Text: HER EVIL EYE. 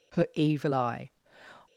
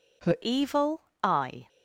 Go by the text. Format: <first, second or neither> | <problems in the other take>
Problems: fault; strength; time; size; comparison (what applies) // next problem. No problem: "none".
first | changes voice at "EVIL"; from 0.4 s on; 1.2 s long // pauses between "EVIL" and "EYE"; slight; at 0.9 s; 0.24 s long